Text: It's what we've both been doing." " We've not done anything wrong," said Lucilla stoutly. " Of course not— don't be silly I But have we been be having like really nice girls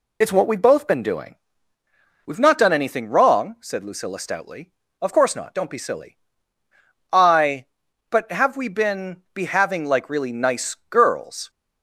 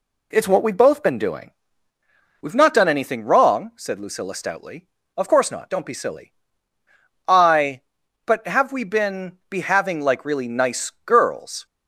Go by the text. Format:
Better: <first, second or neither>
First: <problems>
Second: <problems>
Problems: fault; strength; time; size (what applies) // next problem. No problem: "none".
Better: second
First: loses the start of "It's"; at 0.2 s; 45 ms // pauses between "silly" and "I"; noticeable; at 6.1 s; 0.96 s long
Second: pauses between "silly" and "I"; noticeable; at 6.3 s; 0.96 s long